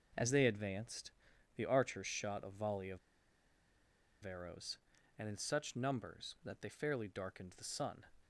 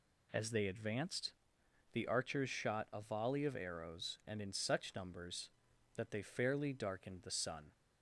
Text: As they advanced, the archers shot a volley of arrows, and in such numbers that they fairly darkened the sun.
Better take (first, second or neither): second